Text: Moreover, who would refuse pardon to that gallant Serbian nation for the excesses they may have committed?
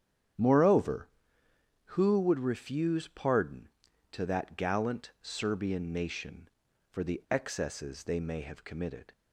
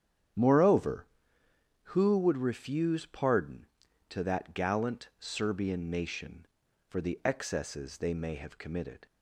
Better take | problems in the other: neither | starts louder than the rest; strong; the same in both

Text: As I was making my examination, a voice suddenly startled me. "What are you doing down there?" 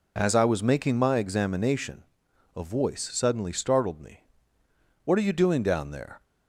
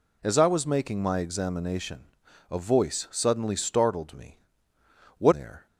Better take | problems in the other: first | skips "are you doing down"; at 5.3 s

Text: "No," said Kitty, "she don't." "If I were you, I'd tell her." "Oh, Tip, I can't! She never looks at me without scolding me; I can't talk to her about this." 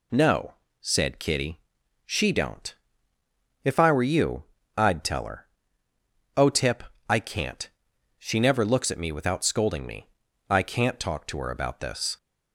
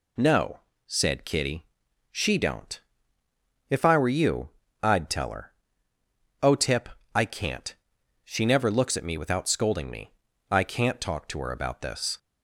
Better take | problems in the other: neither | none

